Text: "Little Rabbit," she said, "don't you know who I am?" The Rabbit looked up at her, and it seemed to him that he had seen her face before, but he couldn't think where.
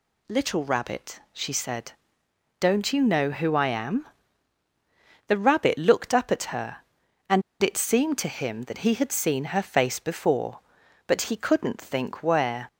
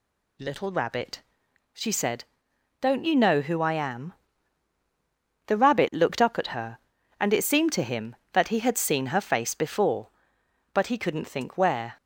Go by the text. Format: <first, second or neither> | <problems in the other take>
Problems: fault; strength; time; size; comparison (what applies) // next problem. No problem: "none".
second | pauses between "and" and "it"; slight; at 7.4 s; 0.21 s long